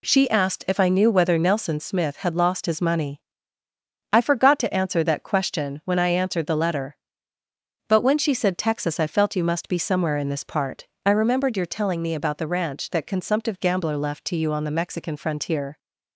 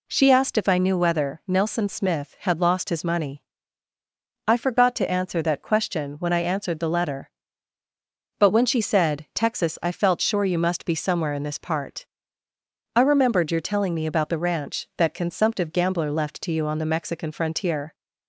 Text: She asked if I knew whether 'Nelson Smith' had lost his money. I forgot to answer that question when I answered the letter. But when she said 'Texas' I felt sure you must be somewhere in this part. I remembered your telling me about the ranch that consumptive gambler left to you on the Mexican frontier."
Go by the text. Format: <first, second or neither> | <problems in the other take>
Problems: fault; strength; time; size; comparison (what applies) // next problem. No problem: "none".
second | skips "sure"; at 9.3 s